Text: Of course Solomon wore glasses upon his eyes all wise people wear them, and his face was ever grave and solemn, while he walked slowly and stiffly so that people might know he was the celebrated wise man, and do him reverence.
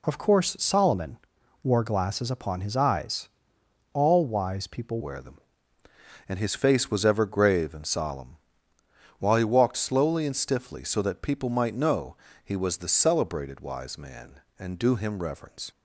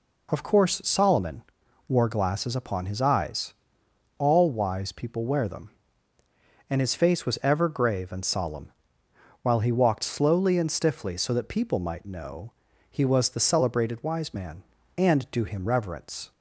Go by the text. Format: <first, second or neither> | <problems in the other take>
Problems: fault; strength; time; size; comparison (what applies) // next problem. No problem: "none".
second | pauses between "Solomon" and "wore"; noticeable; at 1.1 s; 0.46 s long; noticeable in the second // pauses between "eyes" and "all"; noticeable; at 3.2 s; 0.66 s long; noticeable in the second // changes voice at "wear"; from 5.0 s on; 10.7 s long // pauses between "know" and "he"; slight; at 12.1 s; 0.30 s long; also in the second